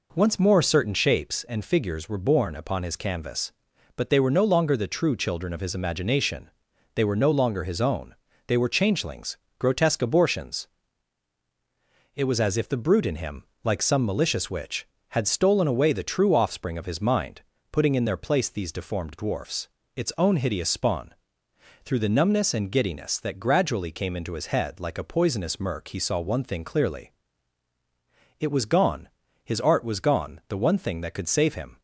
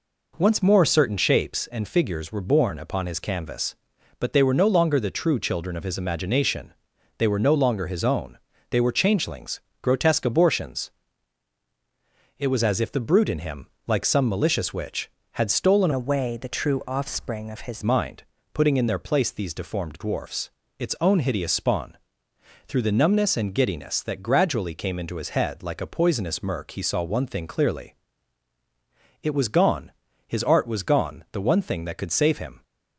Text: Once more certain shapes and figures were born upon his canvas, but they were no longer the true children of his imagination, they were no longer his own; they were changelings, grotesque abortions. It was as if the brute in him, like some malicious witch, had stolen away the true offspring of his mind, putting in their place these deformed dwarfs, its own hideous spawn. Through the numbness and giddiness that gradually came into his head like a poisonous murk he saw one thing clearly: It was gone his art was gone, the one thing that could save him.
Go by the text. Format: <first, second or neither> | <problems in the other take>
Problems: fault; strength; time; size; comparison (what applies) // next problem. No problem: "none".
first | changes voice from "away" to "his"; from 15.9 to 17.8 s; 1.9 s long // pauses between "gone" and "his"; slight; at 29.9 s; 0.34 s long; slight in the first